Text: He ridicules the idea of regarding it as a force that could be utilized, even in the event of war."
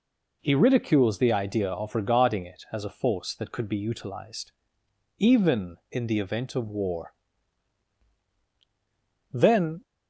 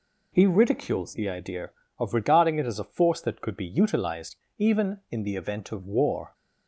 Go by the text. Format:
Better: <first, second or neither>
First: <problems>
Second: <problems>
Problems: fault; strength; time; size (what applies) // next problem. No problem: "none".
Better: second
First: goes on to say "Then"; from 9.3 s on; 0.52 s long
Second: none